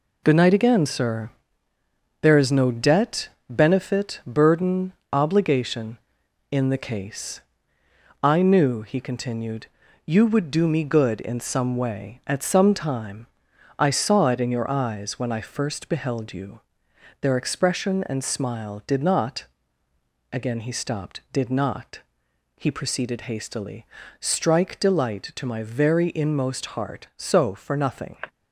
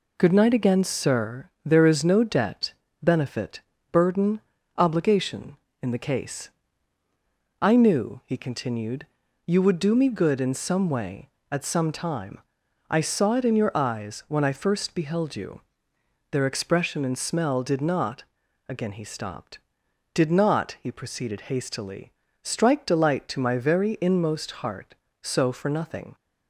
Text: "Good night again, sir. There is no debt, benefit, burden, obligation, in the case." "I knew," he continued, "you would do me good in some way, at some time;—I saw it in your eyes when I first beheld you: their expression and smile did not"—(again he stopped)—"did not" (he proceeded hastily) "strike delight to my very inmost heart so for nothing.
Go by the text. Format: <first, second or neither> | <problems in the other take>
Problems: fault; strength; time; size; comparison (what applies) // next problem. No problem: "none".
first | says "smell" for "smile"; at 17.1 s